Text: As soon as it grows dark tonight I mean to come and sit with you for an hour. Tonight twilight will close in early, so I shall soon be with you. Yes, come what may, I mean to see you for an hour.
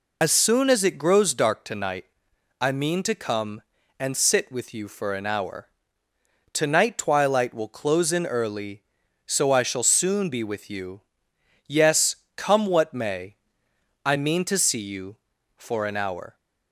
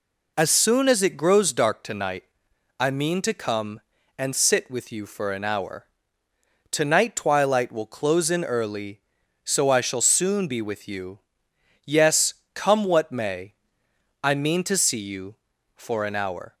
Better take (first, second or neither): second